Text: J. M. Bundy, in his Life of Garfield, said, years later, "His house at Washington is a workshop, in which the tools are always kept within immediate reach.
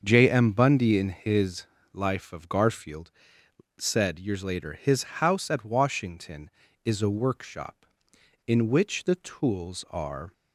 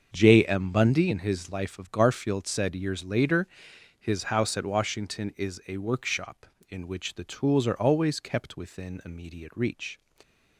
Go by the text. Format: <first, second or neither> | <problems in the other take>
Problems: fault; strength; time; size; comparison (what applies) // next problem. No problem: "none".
second | starts louder than the rest; until 1.0 s; 6.5 dB; also in the second // pauses between "his" and "Life"; slight; at 1.6 s; 0.28 s long // stops before "always kept within immediate reach"; at 10.3 s